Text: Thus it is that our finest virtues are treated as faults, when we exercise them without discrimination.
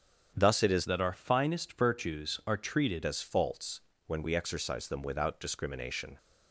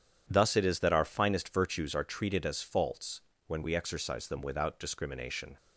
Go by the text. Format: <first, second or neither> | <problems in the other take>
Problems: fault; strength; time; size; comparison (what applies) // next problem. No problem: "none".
second | starts louder than the rest; strong; until 1.3 s; 8 dB // changes voice from "that" to "treated"; from 0.8 to 3.0 s; 2.2 s long